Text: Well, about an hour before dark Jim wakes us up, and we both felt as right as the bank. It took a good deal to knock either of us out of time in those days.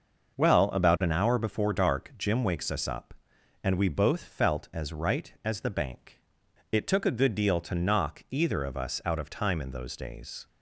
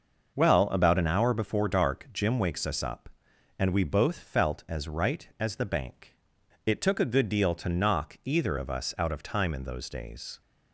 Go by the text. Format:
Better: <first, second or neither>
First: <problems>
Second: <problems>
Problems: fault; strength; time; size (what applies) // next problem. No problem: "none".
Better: neither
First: starts louder than the rest; until 1.4 s; 6 dB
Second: starts louder than the rest; until 1.4 s; 6 dB